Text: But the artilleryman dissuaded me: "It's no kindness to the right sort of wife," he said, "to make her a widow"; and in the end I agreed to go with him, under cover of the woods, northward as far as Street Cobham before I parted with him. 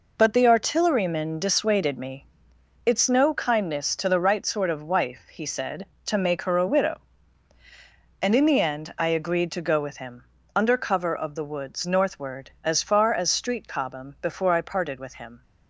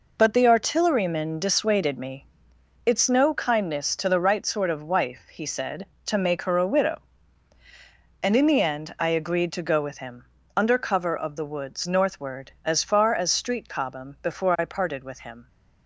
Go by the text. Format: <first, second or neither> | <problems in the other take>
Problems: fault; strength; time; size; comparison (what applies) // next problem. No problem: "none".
neither | none